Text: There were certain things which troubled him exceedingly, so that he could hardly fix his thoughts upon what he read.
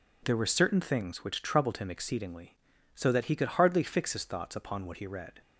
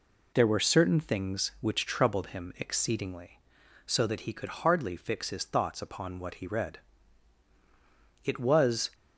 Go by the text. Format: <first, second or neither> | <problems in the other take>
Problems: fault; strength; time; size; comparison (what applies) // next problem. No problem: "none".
first | goes on to say "It was"; noticeable; from 8.2 s on; 0.68 s long